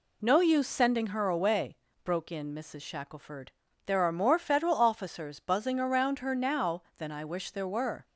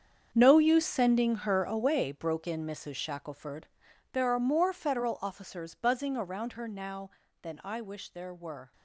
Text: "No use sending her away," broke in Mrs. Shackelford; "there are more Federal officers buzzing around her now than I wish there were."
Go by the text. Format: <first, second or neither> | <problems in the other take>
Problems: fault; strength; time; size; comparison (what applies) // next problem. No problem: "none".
first | gets quieter; strong; throughout; 13.5 dB